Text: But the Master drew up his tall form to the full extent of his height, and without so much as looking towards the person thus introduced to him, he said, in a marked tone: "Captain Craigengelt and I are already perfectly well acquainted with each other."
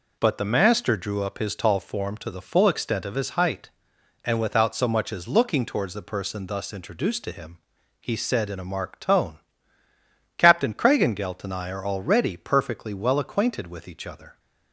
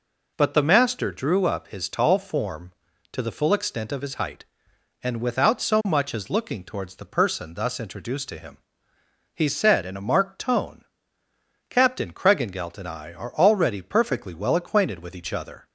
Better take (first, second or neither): neither